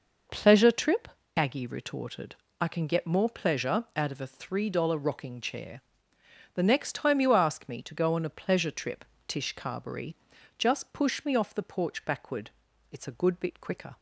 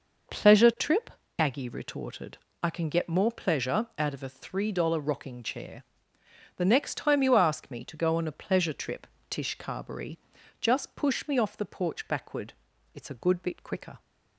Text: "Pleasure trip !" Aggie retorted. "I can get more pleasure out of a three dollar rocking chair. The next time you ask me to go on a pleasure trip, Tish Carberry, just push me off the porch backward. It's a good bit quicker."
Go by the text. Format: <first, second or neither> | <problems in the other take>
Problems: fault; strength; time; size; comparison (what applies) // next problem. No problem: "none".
neither | none